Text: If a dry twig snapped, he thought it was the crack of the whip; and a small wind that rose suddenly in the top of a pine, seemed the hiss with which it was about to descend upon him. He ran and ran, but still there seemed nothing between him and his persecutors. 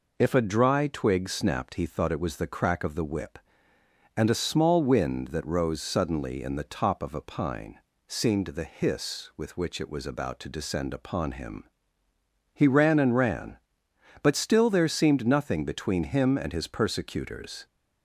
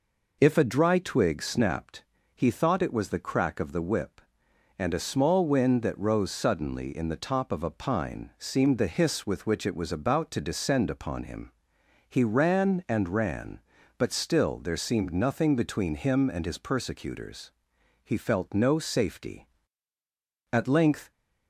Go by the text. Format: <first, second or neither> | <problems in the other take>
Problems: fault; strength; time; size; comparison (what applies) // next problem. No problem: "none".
first | goes on to say "He felt no safety At length"; strong; from 18.0 s on; 3.0 s long